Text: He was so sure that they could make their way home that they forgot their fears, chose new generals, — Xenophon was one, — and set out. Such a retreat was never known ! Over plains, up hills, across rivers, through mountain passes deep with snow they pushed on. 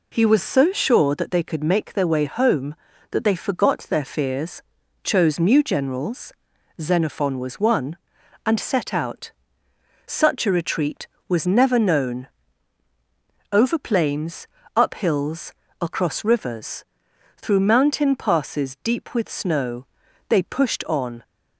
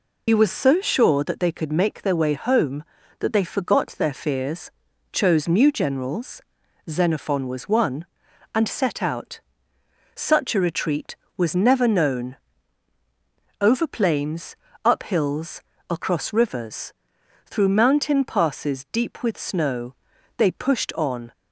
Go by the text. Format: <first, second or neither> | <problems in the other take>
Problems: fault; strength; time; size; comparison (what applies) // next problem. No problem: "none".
first | loses the start of "He"; at 0.2 s; 75 ms // pauses between "snow" and "they"; at 19.9 s; 0.42 s long; also in the first